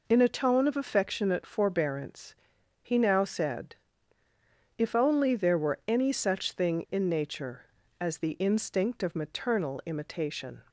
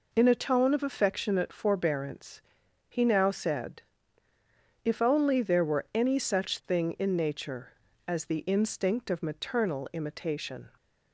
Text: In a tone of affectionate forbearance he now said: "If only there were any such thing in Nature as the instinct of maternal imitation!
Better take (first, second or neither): neither